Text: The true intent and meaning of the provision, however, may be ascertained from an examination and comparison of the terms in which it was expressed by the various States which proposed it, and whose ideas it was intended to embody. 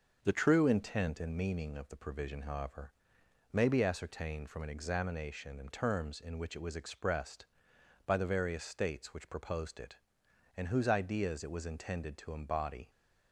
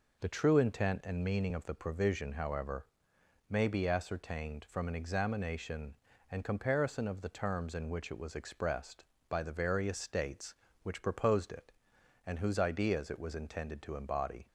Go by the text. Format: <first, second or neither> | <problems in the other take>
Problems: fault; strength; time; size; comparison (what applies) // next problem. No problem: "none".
second | starts louder than the rest; until 1.2 s; 6 dB // skips "comparison of the"; at 5.7 s